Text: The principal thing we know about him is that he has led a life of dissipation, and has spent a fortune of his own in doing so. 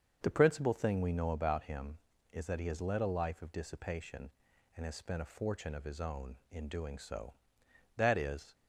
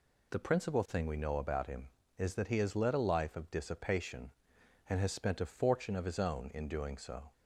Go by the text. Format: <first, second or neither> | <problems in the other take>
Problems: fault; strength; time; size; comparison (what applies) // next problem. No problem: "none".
second | starts louder than the rest; until 1.2 s; 7 dB // goes on to say "That is"; from 7.9 s on; 0.58 s long